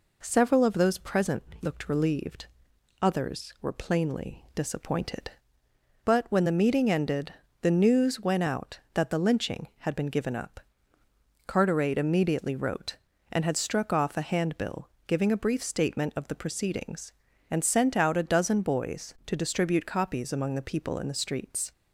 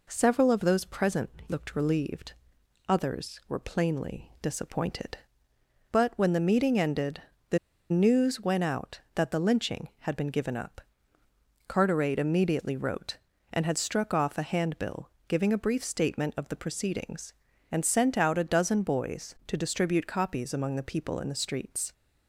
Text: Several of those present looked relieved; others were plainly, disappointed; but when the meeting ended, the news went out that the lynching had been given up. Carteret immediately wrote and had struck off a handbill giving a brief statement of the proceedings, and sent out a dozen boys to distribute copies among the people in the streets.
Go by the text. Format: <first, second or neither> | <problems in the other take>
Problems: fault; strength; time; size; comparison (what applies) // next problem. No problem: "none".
first | pauses between "present" and "looked"; slight; at 1.3 s; 0.18 s long; slight in the first // pauses between "the" and "news"; slight; at 7.5 s; 0.32 s long // pauses between "handbill" and "giving"; slight; at 15.1 s; 0.18 s long; slight in the first